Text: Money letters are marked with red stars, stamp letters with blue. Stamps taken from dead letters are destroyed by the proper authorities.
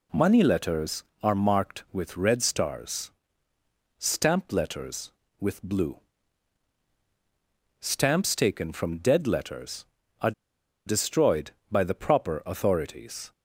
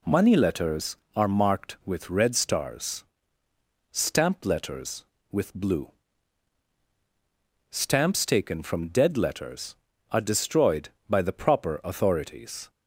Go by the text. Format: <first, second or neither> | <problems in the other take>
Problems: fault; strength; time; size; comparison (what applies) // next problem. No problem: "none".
second | pauses between "are" and "destroyed"; noticeable; at 10.3 s; 0.54 s long